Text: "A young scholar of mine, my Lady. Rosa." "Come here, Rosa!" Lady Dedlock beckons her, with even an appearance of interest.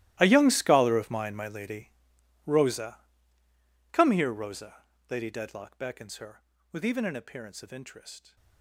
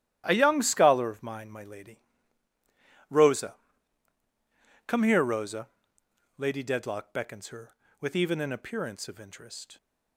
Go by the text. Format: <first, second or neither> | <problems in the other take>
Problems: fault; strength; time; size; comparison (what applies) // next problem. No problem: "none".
second | gets quieter; strong; throughout; 20 dB // starts louder than the rest; strong; until 1.2 s; 15.5 dB; strong in the second